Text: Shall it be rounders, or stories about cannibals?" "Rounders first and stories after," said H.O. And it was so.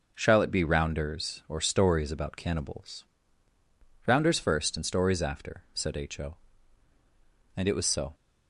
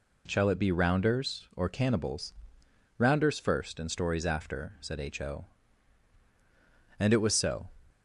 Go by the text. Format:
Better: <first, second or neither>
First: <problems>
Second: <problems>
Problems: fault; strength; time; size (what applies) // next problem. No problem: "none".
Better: first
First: none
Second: skips "stories about"; at 1.6 s